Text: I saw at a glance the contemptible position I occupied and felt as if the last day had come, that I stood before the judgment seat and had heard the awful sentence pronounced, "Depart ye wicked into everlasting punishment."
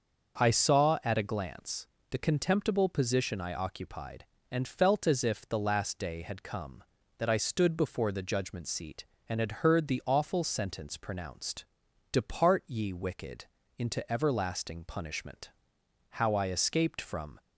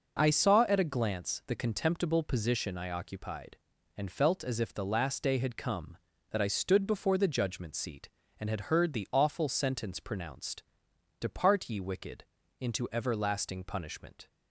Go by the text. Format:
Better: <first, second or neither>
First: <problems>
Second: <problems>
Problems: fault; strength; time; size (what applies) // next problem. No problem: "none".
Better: second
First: starts louder than the rest; until 1.4 s; 6.5 dB // pauses between "glance" and "the"; slight; at 1.8 s; 0.24 s long // pauses between "wicked" and "into"; slight; at 13.4 s; 0.32 s long // goes on to say "How I escaped from"; noticeable; from 16.1 s on; 1.3 s long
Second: pauses between "wicked" and "into"; slight; at 12.2 s; 0.36 s long